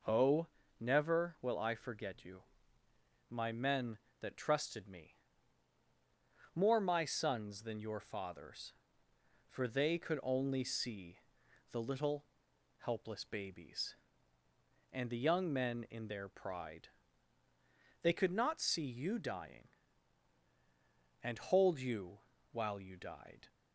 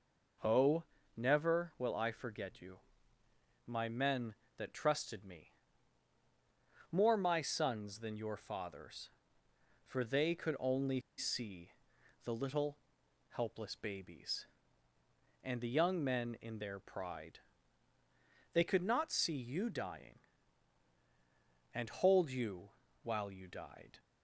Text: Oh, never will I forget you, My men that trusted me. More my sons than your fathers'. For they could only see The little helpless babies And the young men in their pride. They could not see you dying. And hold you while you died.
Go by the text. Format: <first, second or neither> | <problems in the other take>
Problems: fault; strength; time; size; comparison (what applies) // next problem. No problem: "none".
first | pauses between "only" and "see"; slight; at 10.9 s; 0.18 s long // pauses between "see" and "The"; noticeable; at 11.7 s; 0.54 s long; noticeable in the first // pauses between "little" and "helpless"; noticeable; at 12.7 s; 0.52 s long; noticeable in the first // pauses between "you" and "while"; slight; at 22.6 s; 0.32 s long; slight in the first